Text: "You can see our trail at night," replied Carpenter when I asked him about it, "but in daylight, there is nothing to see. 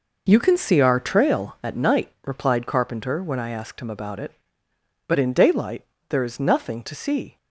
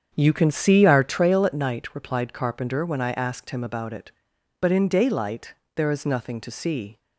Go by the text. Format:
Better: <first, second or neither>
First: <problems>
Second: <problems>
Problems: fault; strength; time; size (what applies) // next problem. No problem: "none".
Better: first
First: none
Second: starts louder than the rest; strong; until 1.2 s; 7.5 dB